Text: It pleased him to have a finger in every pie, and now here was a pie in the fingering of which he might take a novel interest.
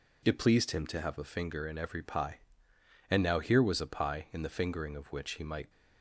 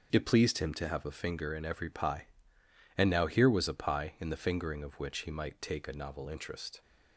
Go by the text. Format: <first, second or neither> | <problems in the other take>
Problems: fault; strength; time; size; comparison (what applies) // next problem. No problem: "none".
second | stops before "take a novel interest"; at 5.7 s